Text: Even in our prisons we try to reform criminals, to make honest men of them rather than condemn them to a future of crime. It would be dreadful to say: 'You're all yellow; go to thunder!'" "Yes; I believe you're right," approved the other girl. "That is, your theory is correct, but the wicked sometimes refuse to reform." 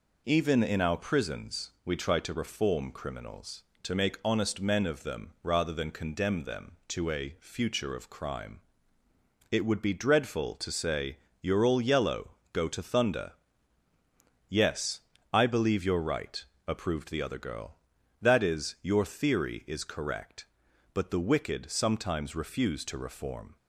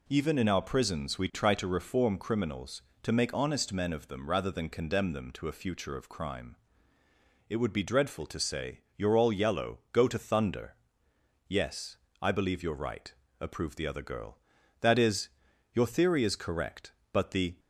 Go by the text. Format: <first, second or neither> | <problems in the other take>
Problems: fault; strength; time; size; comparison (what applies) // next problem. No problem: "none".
first | stops before "wicked sometimes refuse to reform"; at 17.5 s